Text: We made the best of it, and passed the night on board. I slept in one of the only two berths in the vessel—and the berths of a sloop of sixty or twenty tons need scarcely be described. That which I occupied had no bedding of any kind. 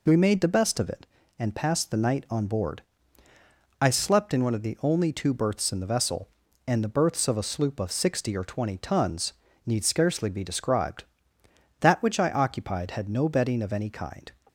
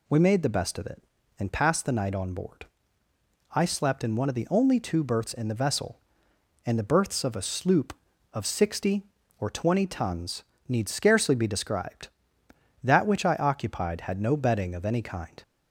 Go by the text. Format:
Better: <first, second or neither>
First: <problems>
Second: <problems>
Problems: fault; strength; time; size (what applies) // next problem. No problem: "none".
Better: neither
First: pauses between "tons" and "need"; slight; at 9.3 s; 0.34 s long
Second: pauses between "tons" and "need"; slight; at 10.4 s; 0.24 s long